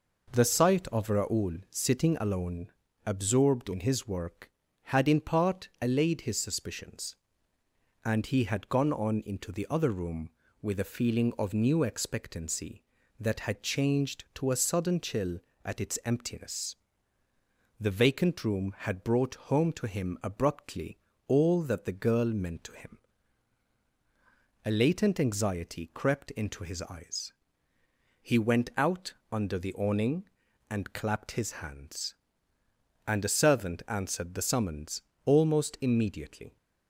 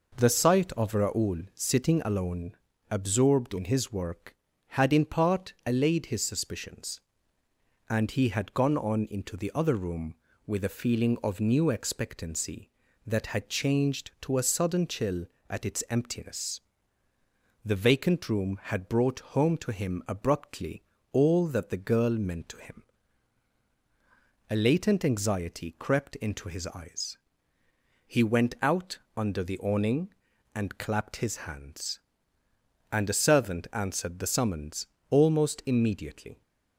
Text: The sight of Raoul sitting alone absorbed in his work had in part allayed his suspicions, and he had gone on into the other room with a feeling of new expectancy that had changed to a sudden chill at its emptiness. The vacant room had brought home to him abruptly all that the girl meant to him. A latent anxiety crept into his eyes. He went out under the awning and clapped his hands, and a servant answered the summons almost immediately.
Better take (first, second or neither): neither